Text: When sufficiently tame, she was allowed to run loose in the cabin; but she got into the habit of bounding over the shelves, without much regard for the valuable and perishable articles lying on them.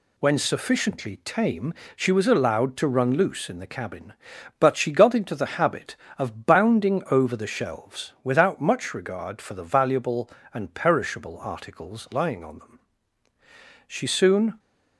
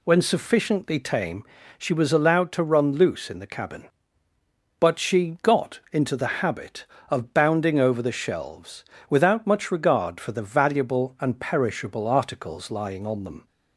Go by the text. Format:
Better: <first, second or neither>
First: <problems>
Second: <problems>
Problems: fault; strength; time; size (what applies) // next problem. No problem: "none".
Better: second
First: goes on to say "She soon"; noticeable; from 13.8 s on; 0.72 s long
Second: none